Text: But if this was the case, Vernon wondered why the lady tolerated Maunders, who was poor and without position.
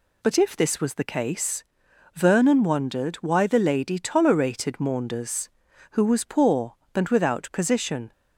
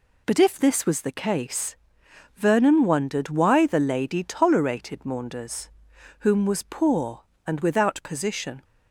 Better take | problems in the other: first | says "whom" for "who"; at 6.1 s

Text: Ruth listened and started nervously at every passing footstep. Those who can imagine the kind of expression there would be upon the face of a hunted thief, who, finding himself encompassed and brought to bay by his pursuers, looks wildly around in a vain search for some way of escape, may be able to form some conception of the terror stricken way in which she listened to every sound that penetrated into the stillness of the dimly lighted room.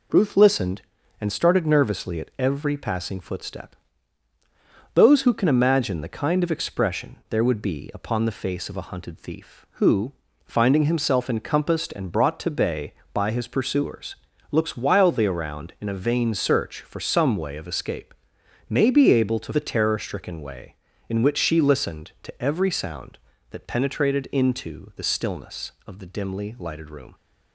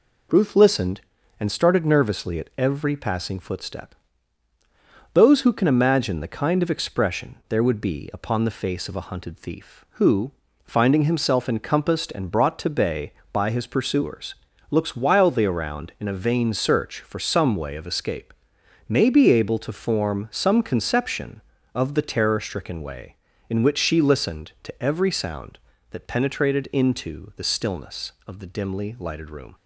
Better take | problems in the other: second | skips "form some conception of"; at 19.5 s

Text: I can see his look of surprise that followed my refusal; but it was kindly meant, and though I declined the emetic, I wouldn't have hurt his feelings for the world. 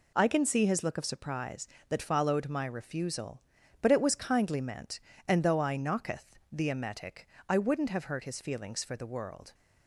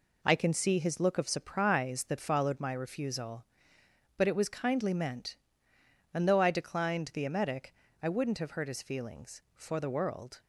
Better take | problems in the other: second | says "knocketh" for "declined"; at 5.7 s

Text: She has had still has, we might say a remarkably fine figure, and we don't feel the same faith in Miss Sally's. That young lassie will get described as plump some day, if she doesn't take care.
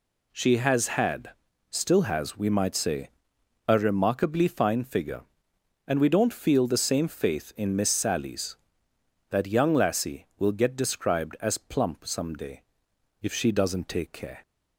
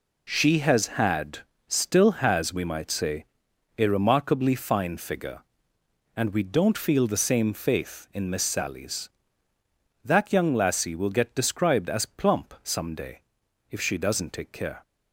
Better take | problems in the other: neither | pauses between "had" and "still"; the same in both // pauses between "say" and "a"; noticeable; the same in both

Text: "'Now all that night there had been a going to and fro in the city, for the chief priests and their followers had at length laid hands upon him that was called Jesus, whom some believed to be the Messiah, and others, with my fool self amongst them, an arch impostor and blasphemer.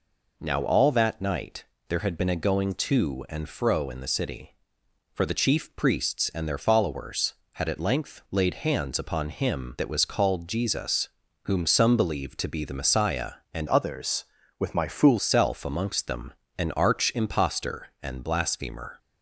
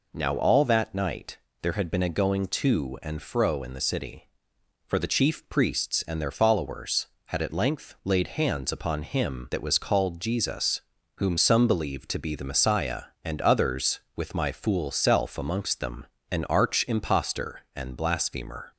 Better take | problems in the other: second | pauses between "night" and "there"; slight; at 1.6 s; 0.24 s long; slight in the second // changes voice from "others" to "fool"; from 13.6 to 15.1 s; 1.5 s long

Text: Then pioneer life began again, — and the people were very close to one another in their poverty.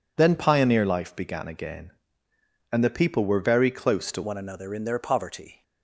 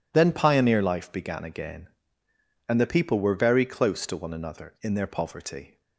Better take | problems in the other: second | changes voice at "one"; from 4.2 s on; 1.4 s long

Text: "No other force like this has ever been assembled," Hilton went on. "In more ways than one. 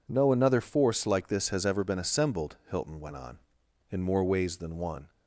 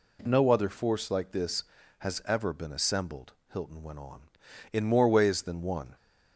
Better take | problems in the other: second | says "another" for "other"; at 0.3 s

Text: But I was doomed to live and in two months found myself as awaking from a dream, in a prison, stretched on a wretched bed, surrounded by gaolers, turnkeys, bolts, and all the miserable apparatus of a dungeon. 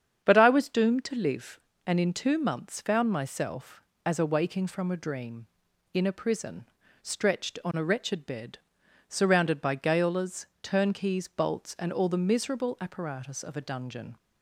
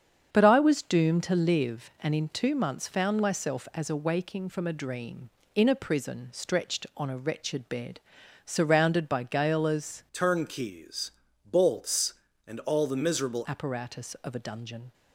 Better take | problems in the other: first | starts louder than the rest; strong; until 1.3 s; 7.5 dB; strong in the first // changes voice from "turnkeys" to "miserable"; from 10.1 to 13.4 s; 3.3 s long

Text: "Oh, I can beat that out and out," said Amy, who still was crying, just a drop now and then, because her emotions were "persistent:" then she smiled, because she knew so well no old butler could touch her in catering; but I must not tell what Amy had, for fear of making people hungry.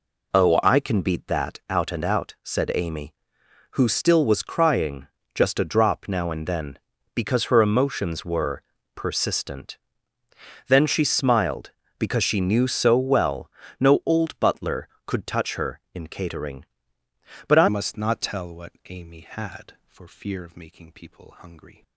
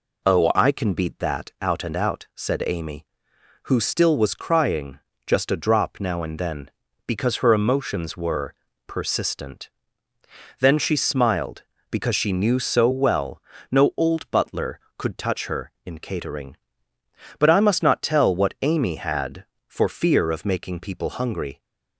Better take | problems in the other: second | pauses between "were" and "persistent"; slight; at 8.6 s; 0.32 s long; slight in the second // pauses between "well" and "no"; slight; at 13.5 s; 0.30 s long; slight in the second // changes voice at "must"; from 17.6 s on; 4.2 s long // pauses between "what" and "Amy"; slight; at 18.7 s; 0.18 s long

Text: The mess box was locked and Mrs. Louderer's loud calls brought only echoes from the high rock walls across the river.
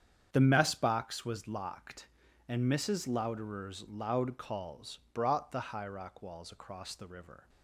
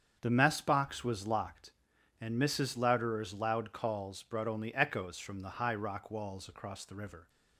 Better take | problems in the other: second | starts louder than the rest; strong; until 1.3 s; 8 dB; strong in the second // pauses between "calls" and "brought"; slight; at 4.9 s; 0.16 s long // skips "only echoes from"; at 5.5 s

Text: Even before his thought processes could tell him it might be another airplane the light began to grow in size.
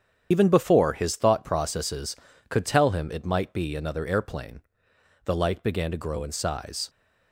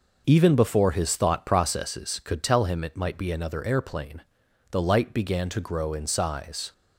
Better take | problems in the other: second | loses the start of "Even"; at 0.3 s; 95 ms // starts louder than the rest; strong; until 1.3 s; 8.5 dB // pauses between "airplane" and "the"; noticeable; at 4.6 s; 0.64 s long; noticeable in the second

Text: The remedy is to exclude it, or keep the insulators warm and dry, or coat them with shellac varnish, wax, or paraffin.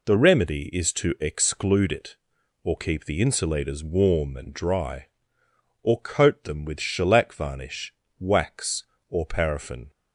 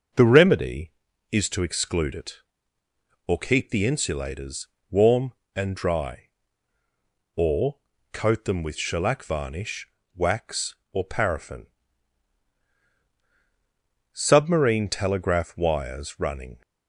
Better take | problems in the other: first | starts louder than the rest; until 1.5 s; 6.5 dB // pauses between "insulators" and "warm"; slight; at 4.6 s; 0.22 s long // pauses between "or" and "coat"; slight; at 7.7 s; 0.34 s long // goes on to say "Submarine telegraph wires running"; strong; from 14.1 s on; 2.5 s long

